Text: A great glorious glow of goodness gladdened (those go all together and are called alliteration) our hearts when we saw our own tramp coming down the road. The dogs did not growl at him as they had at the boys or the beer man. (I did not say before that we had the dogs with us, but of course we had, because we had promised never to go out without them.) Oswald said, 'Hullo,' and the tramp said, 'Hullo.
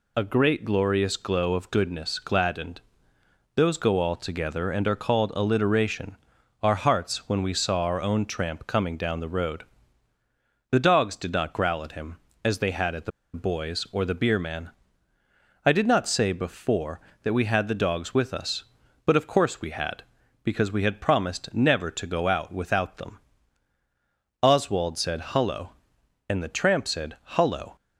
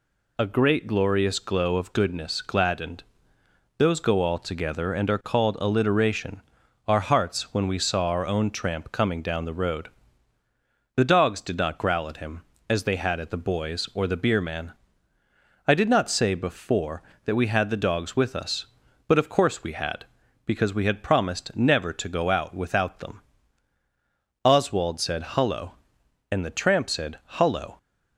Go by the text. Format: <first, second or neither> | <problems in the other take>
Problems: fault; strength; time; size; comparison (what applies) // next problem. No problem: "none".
second | pauses between "the" and "boys"; slight; at 13.1 s; 0.24 s long